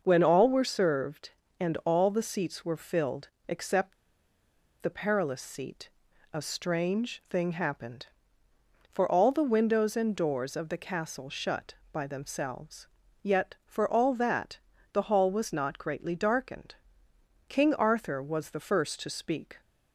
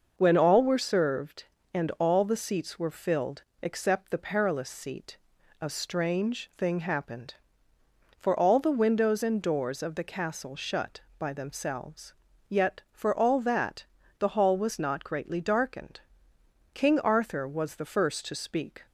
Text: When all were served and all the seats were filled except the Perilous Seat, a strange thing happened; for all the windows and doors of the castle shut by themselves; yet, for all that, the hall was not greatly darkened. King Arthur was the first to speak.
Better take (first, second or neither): second